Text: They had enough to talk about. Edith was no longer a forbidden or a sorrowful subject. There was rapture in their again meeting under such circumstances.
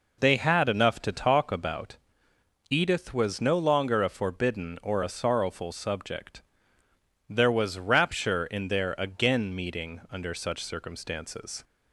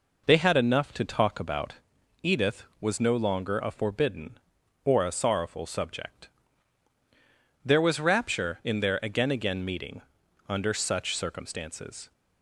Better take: first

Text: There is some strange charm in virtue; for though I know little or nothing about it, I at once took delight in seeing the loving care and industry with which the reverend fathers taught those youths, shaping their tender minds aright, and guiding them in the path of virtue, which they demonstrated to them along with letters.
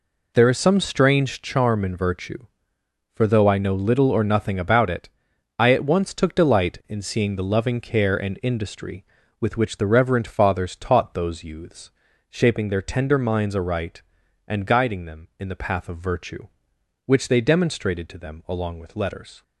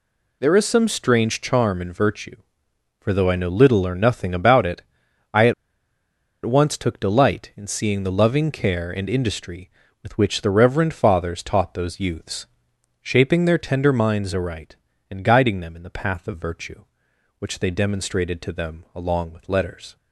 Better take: first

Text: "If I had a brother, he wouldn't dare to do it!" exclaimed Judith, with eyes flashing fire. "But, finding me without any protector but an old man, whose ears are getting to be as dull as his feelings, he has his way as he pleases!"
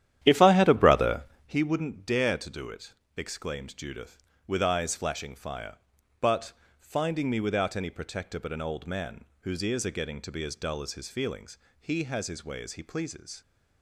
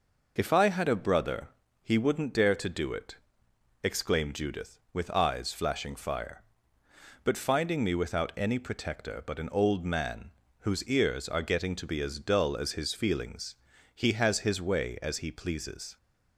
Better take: second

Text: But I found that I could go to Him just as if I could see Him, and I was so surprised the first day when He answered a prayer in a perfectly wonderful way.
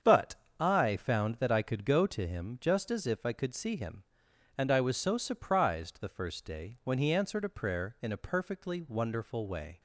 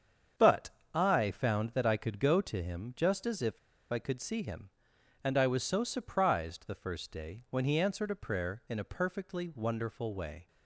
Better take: first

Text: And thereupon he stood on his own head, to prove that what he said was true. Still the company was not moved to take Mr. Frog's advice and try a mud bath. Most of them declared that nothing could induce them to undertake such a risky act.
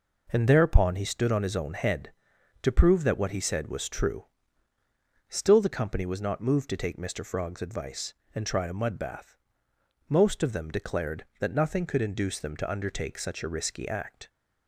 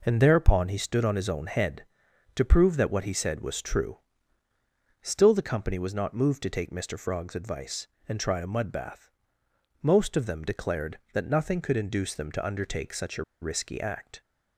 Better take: first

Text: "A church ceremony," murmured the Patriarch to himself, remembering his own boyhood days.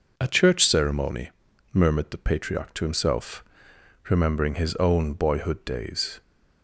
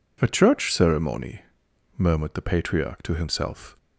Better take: first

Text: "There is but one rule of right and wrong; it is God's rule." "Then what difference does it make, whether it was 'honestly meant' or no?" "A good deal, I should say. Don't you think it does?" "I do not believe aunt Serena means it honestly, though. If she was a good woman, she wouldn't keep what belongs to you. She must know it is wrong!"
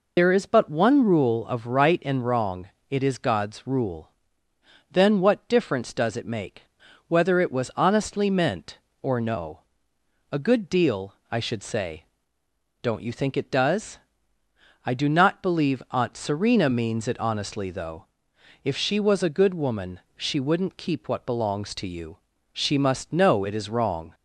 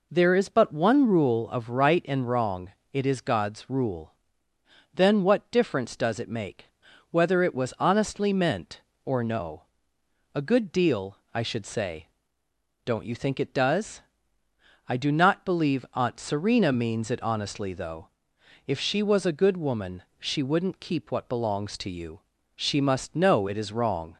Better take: second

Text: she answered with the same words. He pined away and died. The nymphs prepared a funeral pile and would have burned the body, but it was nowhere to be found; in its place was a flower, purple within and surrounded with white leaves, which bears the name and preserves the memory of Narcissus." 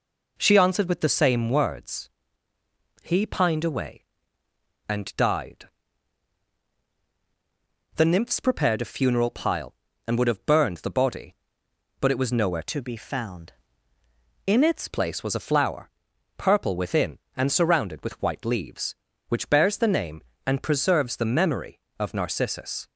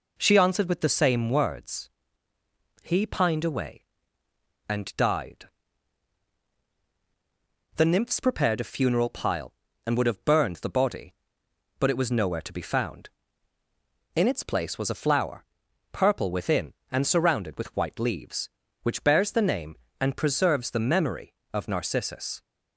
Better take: second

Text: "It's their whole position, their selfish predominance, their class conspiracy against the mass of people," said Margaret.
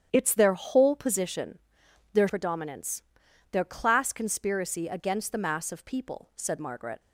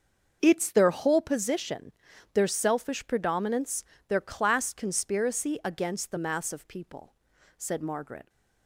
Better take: second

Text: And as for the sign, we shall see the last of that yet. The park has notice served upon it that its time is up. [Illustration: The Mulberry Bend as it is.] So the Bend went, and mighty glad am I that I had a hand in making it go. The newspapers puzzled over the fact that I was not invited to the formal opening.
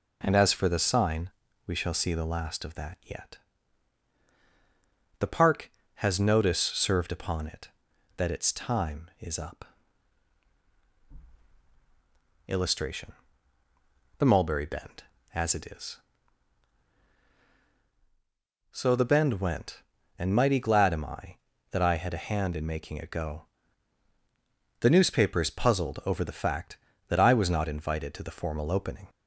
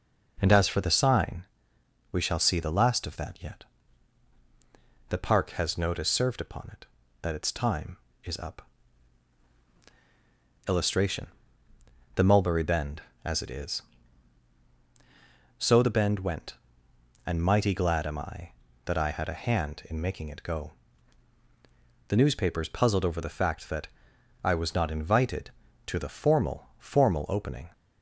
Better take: first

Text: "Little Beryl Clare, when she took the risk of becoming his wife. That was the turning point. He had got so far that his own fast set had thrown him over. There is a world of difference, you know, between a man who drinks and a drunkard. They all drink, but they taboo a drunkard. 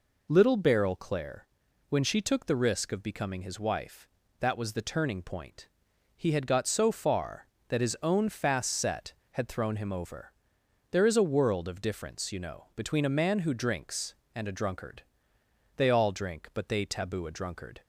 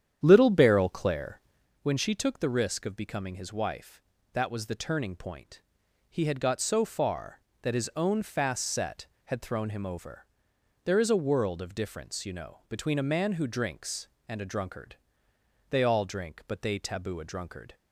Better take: first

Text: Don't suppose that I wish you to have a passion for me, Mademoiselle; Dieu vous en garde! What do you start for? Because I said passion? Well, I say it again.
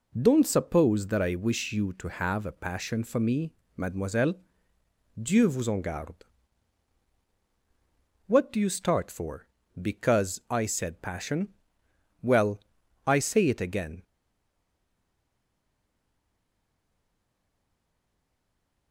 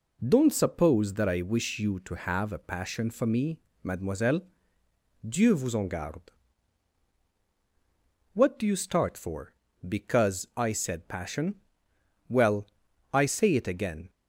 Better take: second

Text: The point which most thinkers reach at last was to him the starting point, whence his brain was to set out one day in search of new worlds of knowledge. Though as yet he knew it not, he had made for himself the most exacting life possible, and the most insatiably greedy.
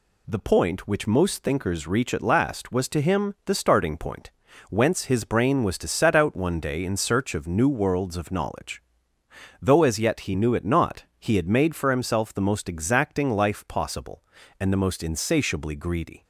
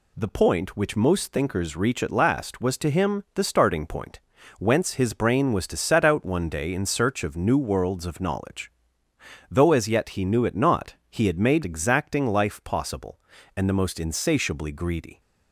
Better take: first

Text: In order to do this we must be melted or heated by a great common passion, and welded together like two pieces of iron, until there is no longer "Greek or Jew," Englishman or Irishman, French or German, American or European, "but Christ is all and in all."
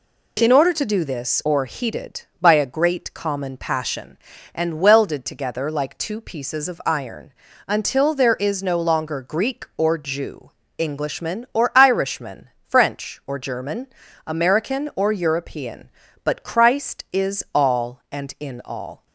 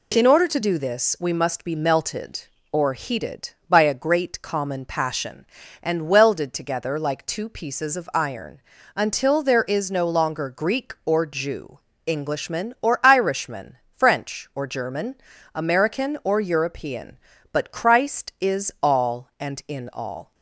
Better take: second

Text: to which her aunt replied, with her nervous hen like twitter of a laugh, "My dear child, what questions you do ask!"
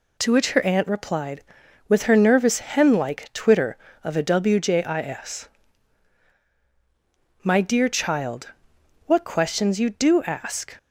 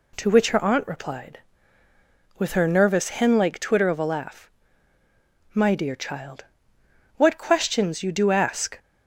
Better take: second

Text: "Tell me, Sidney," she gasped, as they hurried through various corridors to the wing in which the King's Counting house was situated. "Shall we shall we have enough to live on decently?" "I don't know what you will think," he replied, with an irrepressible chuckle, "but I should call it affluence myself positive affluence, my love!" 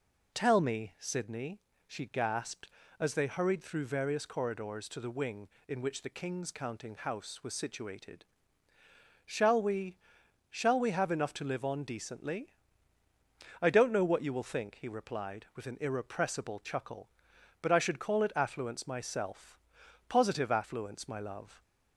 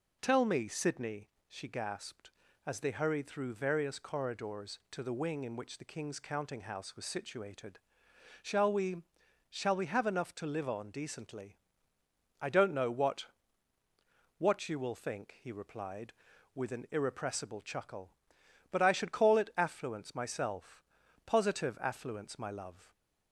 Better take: first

